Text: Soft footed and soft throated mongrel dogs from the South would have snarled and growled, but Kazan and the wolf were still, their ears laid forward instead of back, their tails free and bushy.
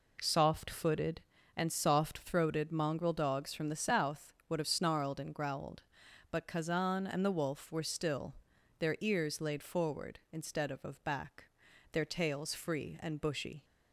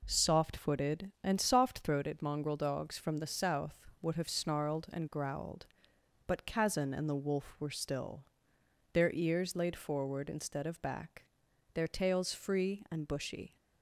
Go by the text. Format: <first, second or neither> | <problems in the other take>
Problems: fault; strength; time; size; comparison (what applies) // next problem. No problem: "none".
second | says "of" twice; at 10.8 s